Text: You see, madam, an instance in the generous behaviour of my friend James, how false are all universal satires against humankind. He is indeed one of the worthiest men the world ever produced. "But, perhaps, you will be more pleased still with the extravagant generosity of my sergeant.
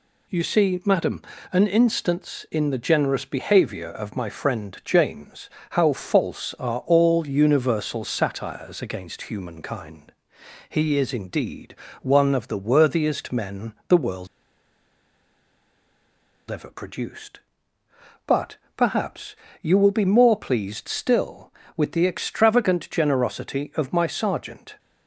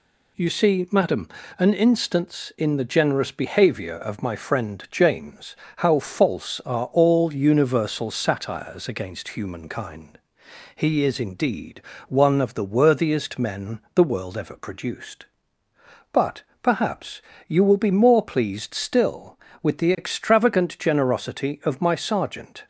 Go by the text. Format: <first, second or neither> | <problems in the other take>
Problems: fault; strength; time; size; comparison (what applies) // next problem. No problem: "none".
second | pauses between "indeed" and "one"; slight; at 11.7 s; 0.28 s long; slight in the second // pauses between "men" and "the"; slight; at 13.7 s; 0.16 s long; slight in the second // pauses between "world" and "ever"; strong; at 14.2 s; 2.2 s long